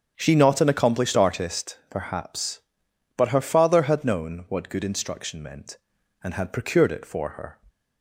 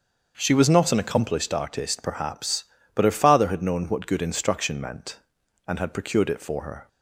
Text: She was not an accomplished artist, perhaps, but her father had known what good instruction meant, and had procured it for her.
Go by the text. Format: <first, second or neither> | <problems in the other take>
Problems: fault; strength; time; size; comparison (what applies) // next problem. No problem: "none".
second | starts louder than the rest; strong; until 1.1 s; 7.5 dB; also in the second // skips "was"; at 0.3 s